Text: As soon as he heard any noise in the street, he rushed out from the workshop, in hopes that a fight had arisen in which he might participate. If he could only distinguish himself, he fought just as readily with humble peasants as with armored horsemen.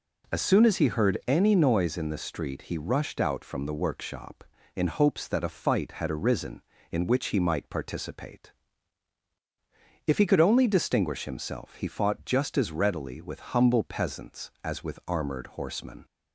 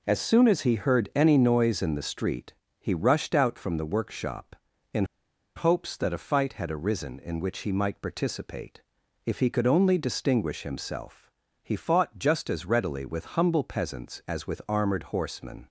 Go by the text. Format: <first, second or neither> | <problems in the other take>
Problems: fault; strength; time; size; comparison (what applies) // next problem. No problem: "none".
first | pauses between "in" and "hopes"; noticeable; at 5.0 s; 0.52 s long